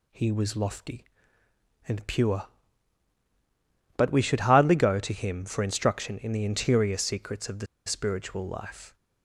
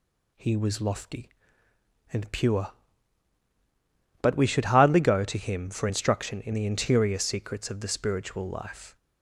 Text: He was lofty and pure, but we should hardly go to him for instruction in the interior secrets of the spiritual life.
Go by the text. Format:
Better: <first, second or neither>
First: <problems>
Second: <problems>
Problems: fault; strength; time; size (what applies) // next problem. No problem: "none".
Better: second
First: pauses between "the" and "spiritual"; slight; at 7.6 s; 0.20 s long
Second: none